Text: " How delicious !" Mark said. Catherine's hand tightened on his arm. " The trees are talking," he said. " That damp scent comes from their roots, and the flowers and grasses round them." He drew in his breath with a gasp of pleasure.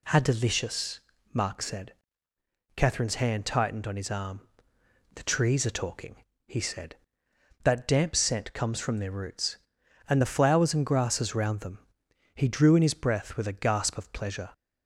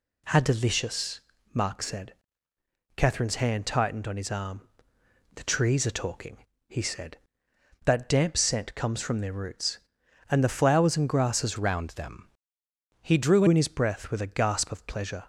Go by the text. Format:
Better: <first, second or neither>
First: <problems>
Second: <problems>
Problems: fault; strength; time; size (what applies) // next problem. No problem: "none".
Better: first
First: none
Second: changes voice from "round" to "drew"; from 11.5 to 13.4 s; 1.9 s long